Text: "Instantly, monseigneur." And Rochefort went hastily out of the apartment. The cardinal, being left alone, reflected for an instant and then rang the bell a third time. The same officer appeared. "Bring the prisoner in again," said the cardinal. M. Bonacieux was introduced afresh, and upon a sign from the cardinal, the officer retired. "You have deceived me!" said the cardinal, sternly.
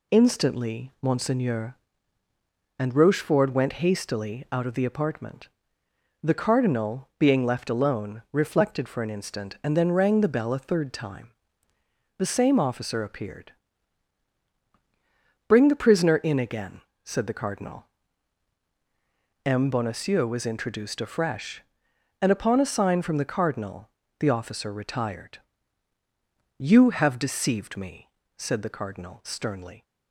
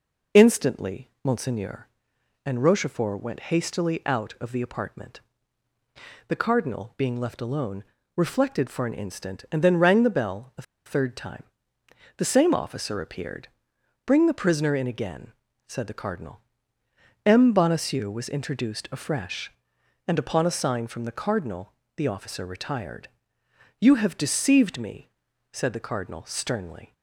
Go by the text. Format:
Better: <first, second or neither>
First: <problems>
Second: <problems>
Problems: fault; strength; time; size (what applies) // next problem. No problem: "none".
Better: first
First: none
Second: pauses between "a" and "third"; slight; at 10.6 s; 0.23 s long